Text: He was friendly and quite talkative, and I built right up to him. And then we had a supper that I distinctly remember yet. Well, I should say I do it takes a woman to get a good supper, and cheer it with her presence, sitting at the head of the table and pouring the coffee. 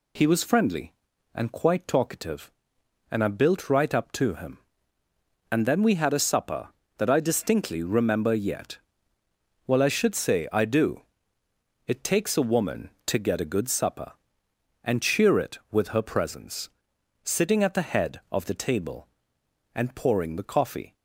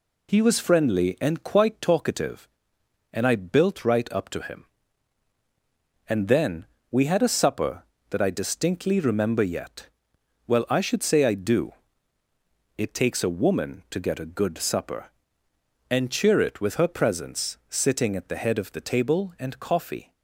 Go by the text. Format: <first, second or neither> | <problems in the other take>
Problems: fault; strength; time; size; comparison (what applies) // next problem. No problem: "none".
first | pauses between "then" and "we"; slight; at 6.6 s; 0.26 s long // pauses between "do" and "it"; at 11.7 s; 1.0 s long; noticeable in the first // skips "pouring the"; at 19.5 s